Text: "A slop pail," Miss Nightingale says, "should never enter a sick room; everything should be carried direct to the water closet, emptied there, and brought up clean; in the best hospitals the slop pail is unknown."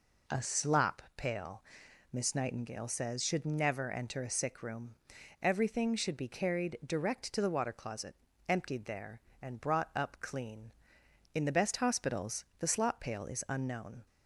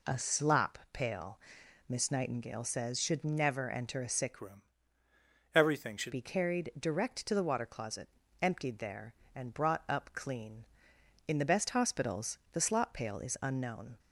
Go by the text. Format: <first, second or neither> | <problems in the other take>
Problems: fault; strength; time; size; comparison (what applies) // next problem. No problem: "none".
first | changes voice from "room" to "should"; from 4.4 to 6.1 s; 1.7 s long